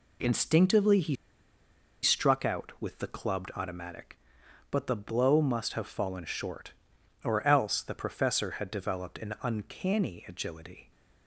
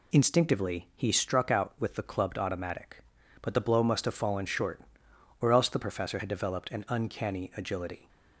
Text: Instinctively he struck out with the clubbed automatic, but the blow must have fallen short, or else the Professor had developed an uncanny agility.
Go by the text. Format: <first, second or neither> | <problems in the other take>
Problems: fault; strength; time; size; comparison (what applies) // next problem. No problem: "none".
second | pauses between "he" and "struck"; noticeable; at 1.1 s; 0.87 s long